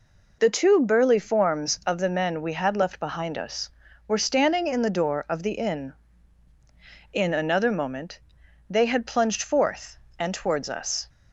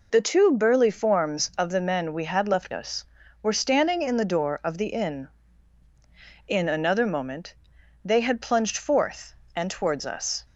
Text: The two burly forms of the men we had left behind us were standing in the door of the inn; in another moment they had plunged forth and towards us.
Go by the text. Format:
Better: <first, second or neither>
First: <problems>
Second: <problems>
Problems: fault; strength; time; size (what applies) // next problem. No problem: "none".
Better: first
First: pauses between "moment" and "they"; noticeable; at 8.2 s; 0.50 s long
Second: skips "behind"; at 2.7 s // pauses between "moment" and "they"; noticeable; at 7.5 s; 0.50 s long